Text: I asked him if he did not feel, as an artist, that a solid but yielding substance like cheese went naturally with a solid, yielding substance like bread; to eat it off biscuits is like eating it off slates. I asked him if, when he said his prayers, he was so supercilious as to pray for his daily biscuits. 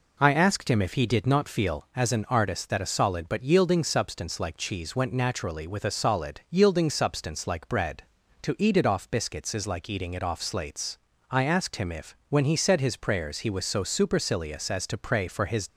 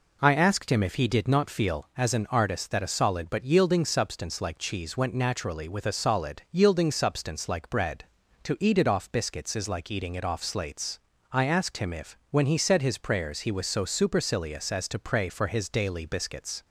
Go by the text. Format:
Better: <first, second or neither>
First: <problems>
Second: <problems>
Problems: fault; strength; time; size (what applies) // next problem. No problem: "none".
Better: second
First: stops before "daily biscuits"; at 15.6 s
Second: none